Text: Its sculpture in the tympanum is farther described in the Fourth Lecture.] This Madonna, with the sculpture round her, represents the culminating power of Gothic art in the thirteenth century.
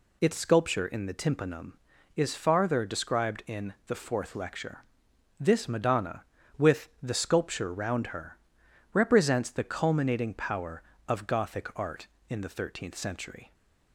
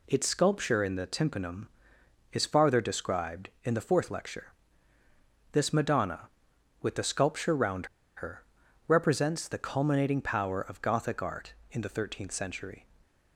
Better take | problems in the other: first | pauses between "round" and "her"; slight; at 7.8 s; 0.29 s long

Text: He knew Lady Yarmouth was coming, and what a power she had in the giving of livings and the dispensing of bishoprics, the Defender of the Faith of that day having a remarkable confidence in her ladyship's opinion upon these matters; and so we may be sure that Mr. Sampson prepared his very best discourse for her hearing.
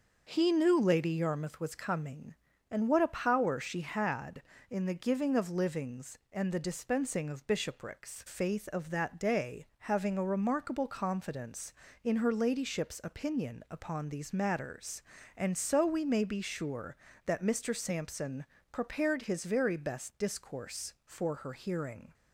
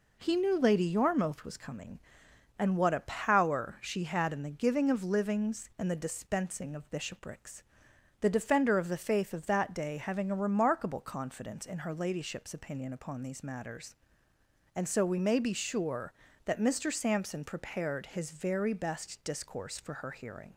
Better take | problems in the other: second | starts louder than the rest; noticeable; until 1.3 s; 6 dB // skips "the Defender of the"; at 8.2 s // pauses between "Sampson" and "prepared"; slight; at 18.4 s; 0.26 s long

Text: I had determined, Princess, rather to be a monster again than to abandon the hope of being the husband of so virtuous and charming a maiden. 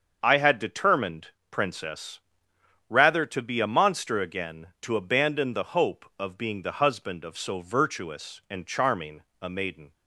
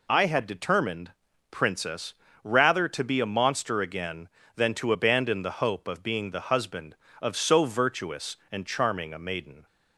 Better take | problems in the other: second | starts louder than the rest; until 1.2 s; 6.5 dB // skips "than"; at 4.7 s // pauses between "charming" and "a"; slight; at 9.2 s; 0.20 s long

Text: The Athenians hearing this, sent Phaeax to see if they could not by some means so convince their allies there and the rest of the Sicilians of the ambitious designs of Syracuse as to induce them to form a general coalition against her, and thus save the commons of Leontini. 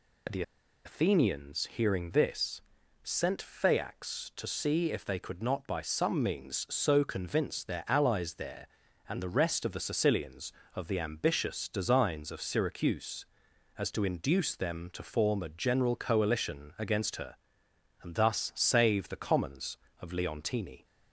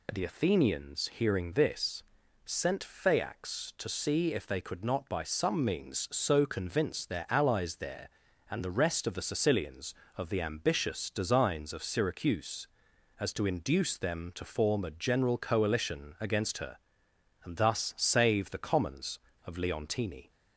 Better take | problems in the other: second | pauses between "The" and "Athenians"; at 0.4 s; 0.43 s long

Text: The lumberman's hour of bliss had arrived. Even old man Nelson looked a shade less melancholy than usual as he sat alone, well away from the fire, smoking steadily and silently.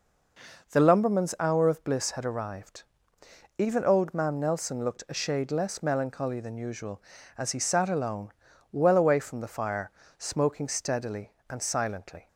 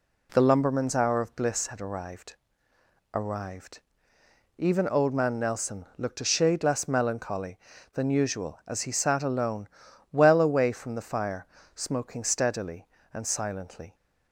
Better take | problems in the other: first | says "arrived" twice; at 3.1 s

